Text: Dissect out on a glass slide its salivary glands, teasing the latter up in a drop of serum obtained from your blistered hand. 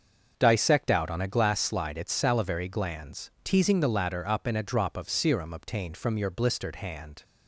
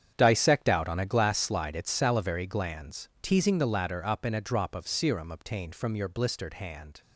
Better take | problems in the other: first | gets quieter; strong; throughout; 13 dB // starts louder than the rest; strong; until 1.1 s; 8.5 dB; also in the first

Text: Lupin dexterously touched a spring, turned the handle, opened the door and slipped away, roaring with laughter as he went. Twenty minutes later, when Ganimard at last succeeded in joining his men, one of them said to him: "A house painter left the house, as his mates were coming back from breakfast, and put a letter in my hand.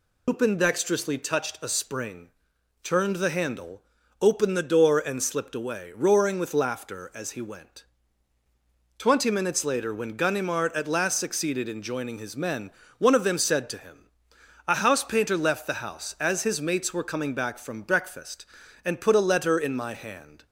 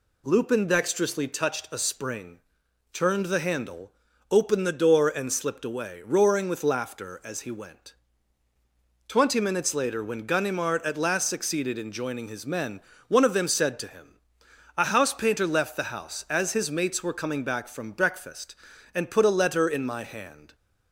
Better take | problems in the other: second | loses the start of "Lupin"; at 0.2 s; 125 ms

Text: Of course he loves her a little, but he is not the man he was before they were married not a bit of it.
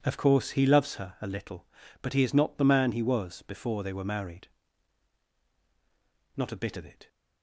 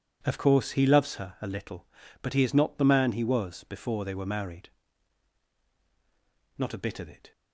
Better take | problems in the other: neither | pauses between "married" and "not"; strong; the same in both

